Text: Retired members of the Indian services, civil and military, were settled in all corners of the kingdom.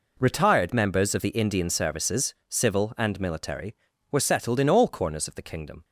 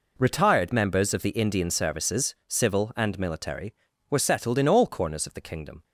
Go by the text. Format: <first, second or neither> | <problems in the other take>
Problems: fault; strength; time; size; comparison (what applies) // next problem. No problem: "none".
neither | none